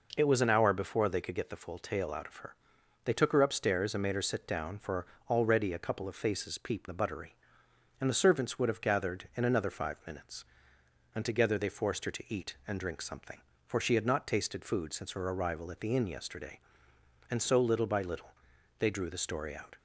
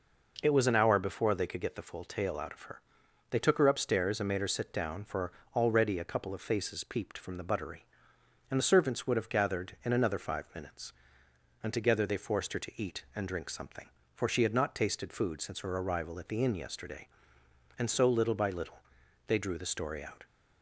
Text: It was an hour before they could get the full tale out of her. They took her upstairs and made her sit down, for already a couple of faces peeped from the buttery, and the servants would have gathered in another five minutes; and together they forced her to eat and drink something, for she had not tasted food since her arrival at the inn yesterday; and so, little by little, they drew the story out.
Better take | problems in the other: second | pauses between "for" and "already"; slight; at 5.0 s; 0.24 s long; slight in the second // skips "from"; at 6.8 s

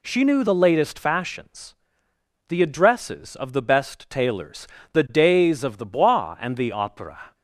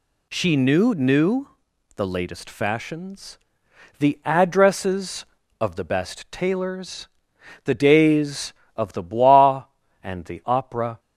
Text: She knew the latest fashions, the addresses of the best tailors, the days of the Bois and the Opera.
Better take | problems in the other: first | says "knew" twice; at 0.9 s

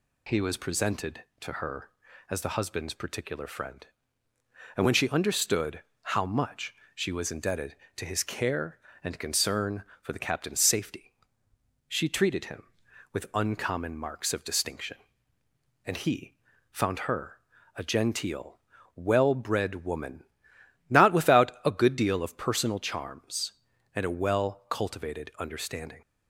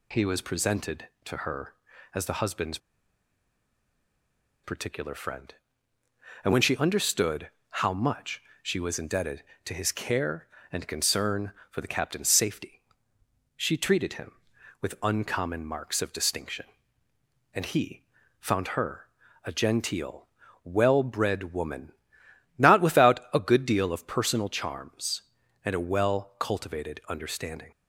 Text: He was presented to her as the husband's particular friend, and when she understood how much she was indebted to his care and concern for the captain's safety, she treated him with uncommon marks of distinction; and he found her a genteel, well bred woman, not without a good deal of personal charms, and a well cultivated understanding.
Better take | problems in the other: first | pauses between "husband's" and "particular"; strong; at 2.7 s; 1.8 s long // pauses between "understood" and "how"; slight; at 7.5 s; 0.18 s long; slight in the first // pauses between "much" and "she"; slight; at 8.4 s; 0.20 s long; slight in the first // pauses between "he" and "found"; at 18.0 s; 0.38 s long; also in the first // pauses between "her" and "a"; at 19.0 s; 0.40 s long; also in the first

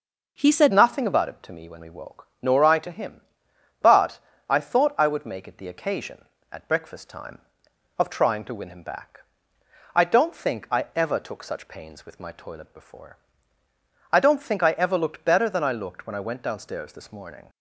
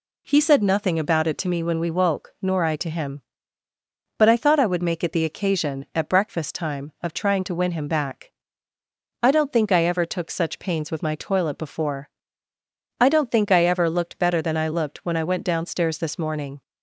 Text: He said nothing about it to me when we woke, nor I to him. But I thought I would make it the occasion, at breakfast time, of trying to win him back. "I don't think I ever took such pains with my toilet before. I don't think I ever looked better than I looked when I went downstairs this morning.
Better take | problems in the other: second | changes voice at "nothing"; from 0.7 s on; 16.7 s long // pauses between "But" and "I"; slight; at 4.1 s; 0.32 s long

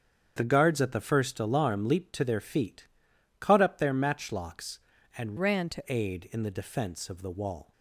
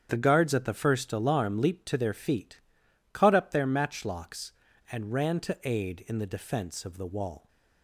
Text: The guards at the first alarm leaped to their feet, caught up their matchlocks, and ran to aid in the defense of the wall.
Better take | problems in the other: second | starts louder than the rest; strong; until 1.3 s; 8 dB; strong in the second // changes voice from "ran" to "to"; from 5.3 to 5.8 s; 0.5 s long

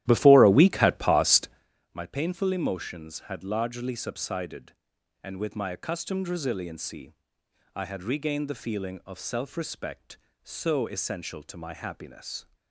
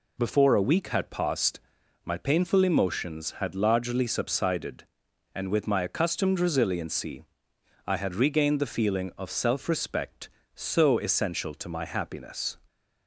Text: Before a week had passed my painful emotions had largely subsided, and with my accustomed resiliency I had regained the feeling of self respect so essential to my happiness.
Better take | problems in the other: second | starts louder than the rest; strong; until 1.7 s; 13.5 dB // pauses between "passed" and "my"; at 1.4 s; 0.44 s long; also in the second // pauses between "resiliency" and "I"; noticeable; at 7.1 s; 0.62 s long; noticeable in the second

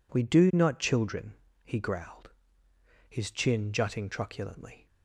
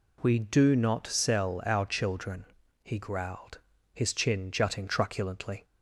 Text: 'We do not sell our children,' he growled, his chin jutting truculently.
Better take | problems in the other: second | skips "sell our"; at 0.7 s

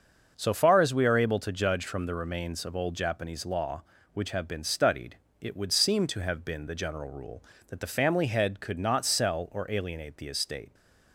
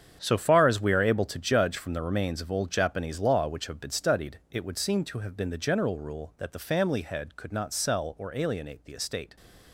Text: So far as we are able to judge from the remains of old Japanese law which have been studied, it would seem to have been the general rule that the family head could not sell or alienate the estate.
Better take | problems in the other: first | gets quieter; strong; throughout; 12 dB // starts louder than the rest; strong; until 1.2 s; 8 dB; also in the first

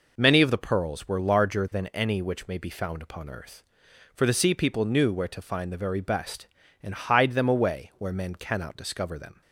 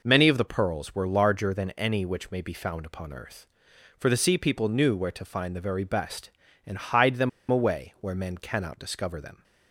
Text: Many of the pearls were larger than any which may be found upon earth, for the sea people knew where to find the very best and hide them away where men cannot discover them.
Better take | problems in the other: first | pauses between "them" and "away"; slight; at 7.2 s; 0.21 s long

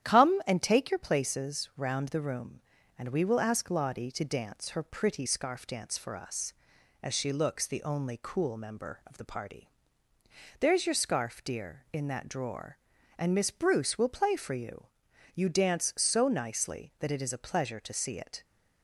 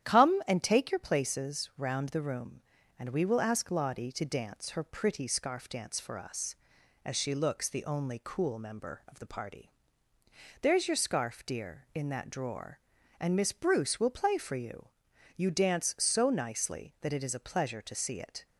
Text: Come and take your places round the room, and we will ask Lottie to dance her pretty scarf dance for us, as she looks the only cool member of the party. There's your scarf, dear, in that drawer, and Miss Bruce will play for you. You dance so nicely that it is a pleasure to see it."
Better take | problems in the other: neither | starts louder than the rest; strong; the same in both

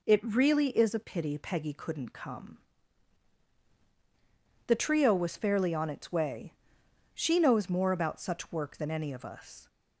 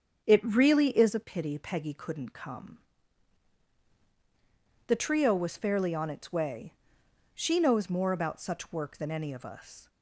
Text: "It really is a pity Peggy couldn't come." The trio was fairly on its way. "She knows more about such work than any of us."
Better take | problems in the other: first | starts louder than the rest; strong; until 1.2 s; 7.5 dB

